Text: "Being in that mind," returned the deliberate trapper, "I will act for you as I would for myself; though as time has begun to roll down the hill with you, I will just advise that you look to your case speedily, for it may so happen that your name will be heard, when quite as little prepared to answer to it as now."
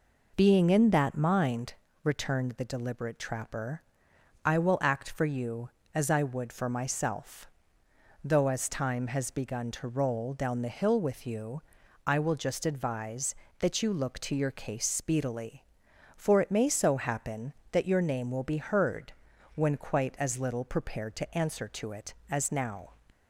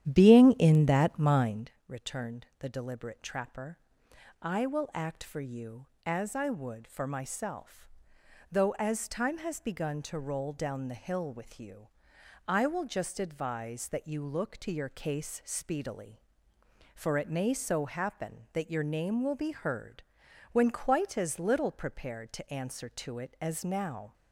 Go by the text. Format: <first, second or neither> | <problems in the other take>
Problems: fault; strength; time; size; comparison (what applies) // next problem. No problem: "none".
first | starts louder than the rest; strong; until 1.7 s; 11 dB